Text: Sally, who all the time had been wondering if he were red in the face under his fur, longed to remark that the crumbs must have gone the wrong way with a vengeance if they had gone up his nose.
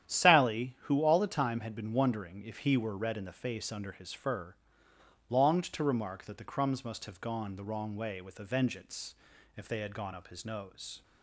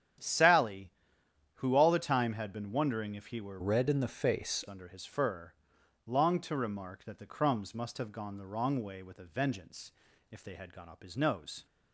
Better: first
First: starts louder than the rest; strong; until 1.1 s; 10 dB // pauses between "vengeance" and "if"; at 9.1 s; 0.42 s long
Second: starts louder than the rest; strong; until 1.8 s; 9.5 dB // changes voice from "red" to "face"; from 3.6 to 4.6 s; 1.0 s long // pauses between "vengeance" and "if"; at 9.9 s; 0.40 s long

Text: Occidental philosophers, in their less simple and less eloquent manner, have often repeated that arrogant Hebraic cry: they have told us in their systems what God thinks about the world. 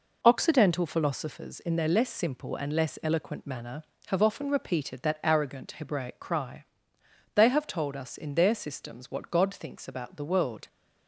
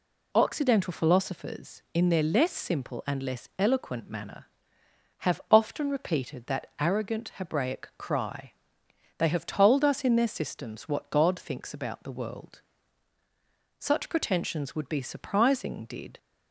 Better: first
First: none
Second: goes on to say "Such pretensions would be surprising did"; strong; from 13.7 s on; 2.4 s long

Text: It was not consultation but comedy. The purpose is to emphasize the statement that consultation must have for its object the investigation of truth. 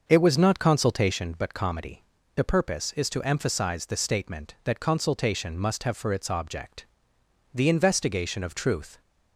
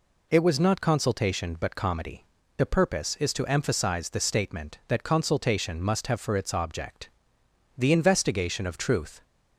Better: second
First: starts louder than the rest; until 1.3 s; 6 dB // pauses between "object" and "the"; noticeable; at 6.8 s; 0.68 s long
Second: pauses between "object" and "the"; noticeable; at 7.0 s; 0.68 s long

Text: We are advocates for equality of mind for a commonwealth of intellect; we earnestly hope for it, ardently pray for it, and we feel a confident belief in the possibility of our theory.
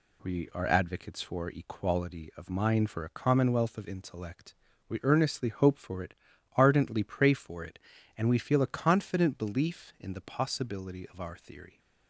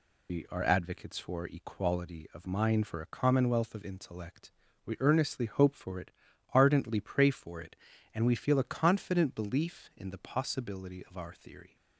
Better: first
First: none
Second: loses the start of "We"; at 0.2 s; 120 ms

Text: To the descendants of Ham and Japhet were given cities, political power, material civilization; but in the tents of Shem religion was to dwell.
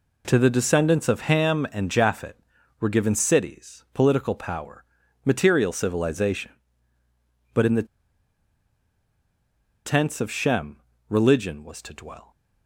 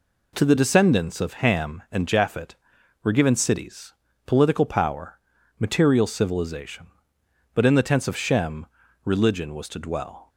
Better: second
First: pauses between "the" and "tents"; strong; at 7.8 s; 1.9 s long // pauses between "Shem" and "religion"; slight; at 10.7 s; 0.34 s long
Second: pauses between "Shem" and "religion"; at 8.6 s; 0.38 s long

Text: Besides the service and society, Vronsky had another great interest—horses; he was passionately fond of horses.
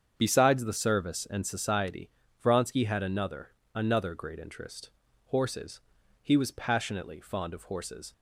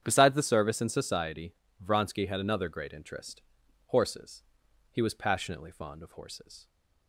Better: second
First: starts louder than the rest; strong; until 1.1 s; 7.5 dB // says "another" twice; at 3.7 s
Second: starts louder than the rest; strong; until 1.0 s; 8.5 dB

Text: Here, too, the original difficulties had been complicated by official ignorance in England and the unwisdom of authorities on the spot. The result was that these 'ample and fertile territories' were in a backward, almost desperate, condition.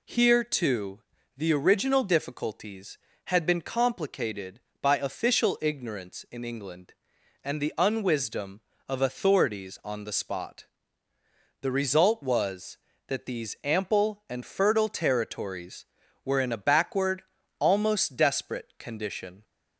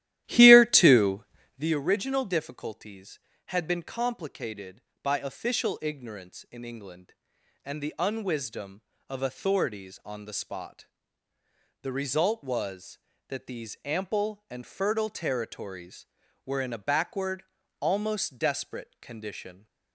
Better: first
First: none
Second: starts louder than the rest; strong; until 1.8 s; 13.5 dB

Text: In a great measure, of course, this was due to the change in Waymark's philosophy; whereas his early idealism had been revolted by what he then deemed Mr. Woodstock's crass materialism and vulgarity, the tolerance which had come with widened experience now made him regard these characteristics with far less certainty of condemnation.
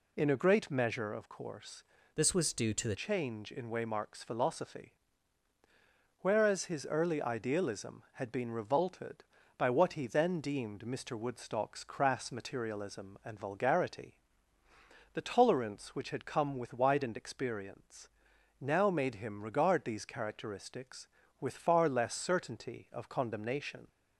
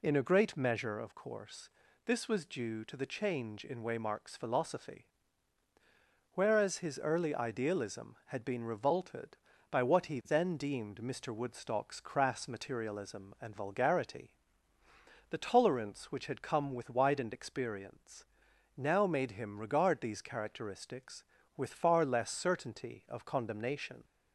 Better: second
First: changes voice from "this" to "the"; from 2.1 to 2.9 s; 0.8 s long // pauses between "experience" and "now"; noticeable; at 18.0 s; 0.54 s long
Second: pauses between "experience" and "now"; noticeable; at 18.2 s; 0.54 s long

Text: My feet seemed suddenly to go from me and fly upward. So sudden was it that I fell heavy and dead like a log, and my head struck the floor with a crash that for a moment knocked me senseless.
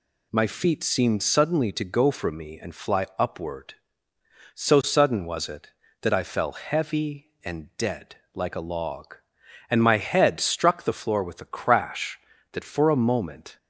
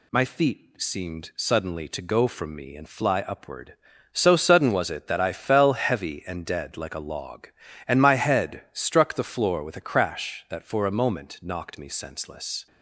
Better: second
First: pauses between "dead" and "like"; slight; at 8.1 s; 0.20 s long // stops before "knocked me senseless"; at 13.5 s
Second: none

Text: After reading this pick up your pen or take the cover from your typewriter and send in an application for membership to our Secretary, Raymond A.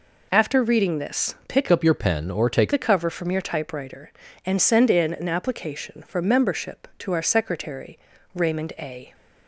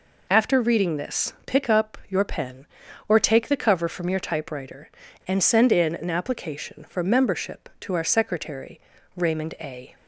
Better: second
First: changes voice from "up" to "take"; from 1.7 to 2.7 s; 1.0 s long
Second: none

